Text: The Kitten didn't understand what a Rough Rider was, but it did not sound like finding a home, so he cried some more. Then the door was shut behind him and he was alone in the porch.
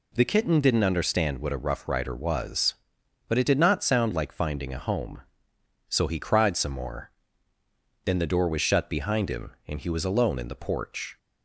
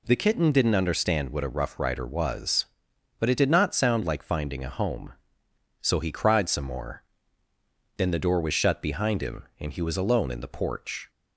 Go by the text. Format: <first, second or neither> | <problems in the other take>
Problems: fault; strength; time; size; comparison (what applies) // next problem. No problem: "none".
neither | none